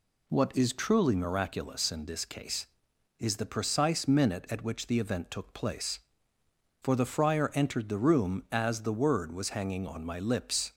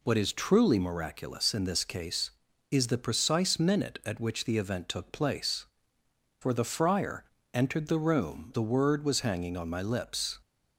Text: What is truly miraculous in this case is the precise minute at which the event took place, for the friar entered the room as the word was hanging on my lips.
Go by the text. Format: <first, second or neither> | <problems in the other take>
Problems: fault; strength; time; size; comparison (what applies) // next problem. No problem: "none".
first | pauses between "friar" and "entered"; slight; at 7.2 s; 0.30 s long // skips "as"; at 8.5 s